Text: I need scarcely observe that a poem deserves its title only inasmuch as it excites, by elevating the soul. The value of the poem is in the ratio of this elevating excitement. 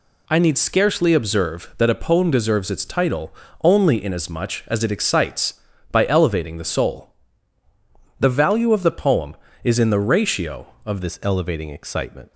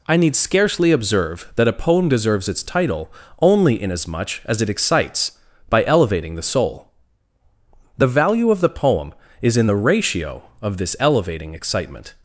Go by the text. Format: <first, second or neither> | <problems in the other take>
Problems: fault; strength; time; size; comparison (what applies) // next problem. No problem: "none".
second | pauses between "title" and "only"; slight; at 3.3 s; 0.30 s long; slight in the second // changes voice at "this"; from 11.0 s on; 1.3 s long